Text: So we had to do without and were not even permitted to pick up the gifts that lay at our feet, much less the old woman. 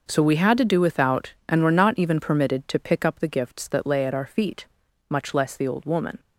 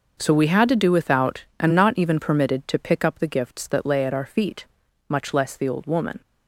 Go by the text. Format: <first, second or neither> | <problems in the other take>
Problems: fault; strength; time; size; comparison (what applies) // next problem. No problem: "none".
first | skips "were"; at 1.7 s